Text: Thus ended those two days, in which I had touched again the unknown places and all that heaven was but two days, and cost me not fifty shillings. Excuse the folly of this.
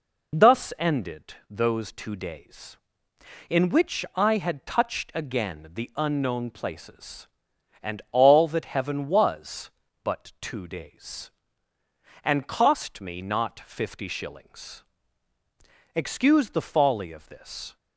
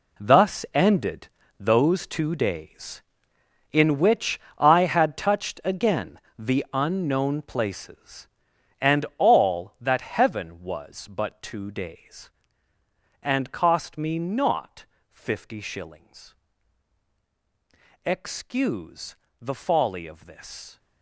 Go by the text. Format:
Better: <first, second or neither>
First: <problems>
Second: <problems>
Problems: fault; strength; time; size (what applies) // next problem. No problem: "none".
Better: first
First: none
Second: gets quieter; strong; throughout; 12 dB // pauses between "ended" and "those"; slight; at 1.2 s; 0.30 s long // pauses between "which" and "I"; slight; at 4.3 s; 0.20 s long // pauses between "again" and "the"; slight; at 6.1 s; 0.20 s long // pauses between "not" and "fifty"; slight; at 14.8 s; 0.24 s long // pauses between "Excuse" and "the"; slight; at 19.1 s; 0.26 s long